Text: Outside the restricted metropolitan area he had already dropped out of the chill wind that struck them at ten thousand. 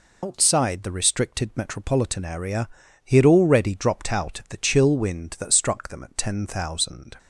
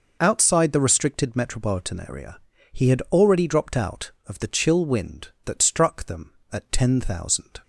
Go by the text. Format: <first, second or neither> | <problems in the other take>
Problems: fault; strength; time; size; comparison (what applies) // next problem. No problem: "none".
second | loses the start of "Outside"; at 0.2 s; 110 ms // pauses between "area" and "he"; slight; at 2.6 s; 0.36 s long; slight in the second